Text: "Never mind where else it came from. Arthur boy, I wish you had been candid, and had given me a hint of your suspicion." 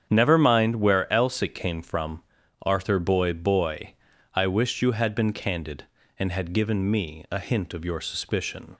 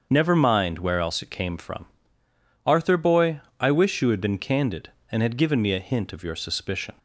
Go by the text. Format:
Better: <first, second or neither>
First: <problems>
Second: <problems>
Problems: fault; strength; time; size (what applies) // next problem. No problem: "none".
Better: second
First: starts louder than the rest; strong; until 1.1 s; 8 dB // says "boy" twice; at 3.3 s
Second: starts louder than the rest; until 1.1 s; 6.5 dB